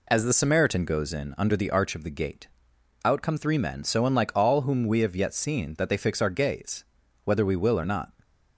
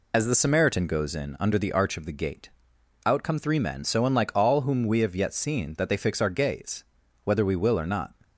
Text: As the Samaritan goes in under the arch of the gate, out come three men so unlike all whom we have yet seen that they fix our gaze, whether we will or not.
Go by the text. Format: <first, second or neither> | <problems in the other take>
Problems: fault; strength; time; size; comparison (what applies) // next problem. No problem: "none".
first | loses the start of "As"; at 0.1 s; 50 ms